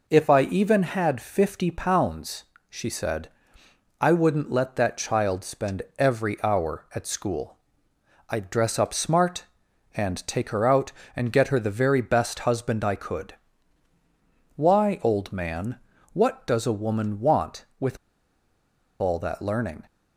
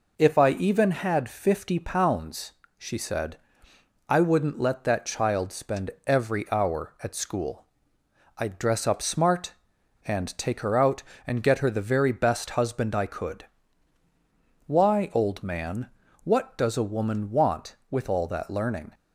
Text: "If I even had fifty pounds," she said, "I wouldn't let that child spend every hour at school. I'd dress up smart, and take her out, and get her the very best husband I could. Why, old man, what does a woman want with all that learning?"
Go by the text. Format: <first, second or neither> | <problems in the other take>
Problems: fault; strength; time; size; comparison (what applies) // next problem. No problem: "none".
second | pauses between "spend" and "every"; slight; at 5.8 s; 0.16 s long; slight in the second // pauses between "with" and "all"; at 17.9 s; 1.0 s long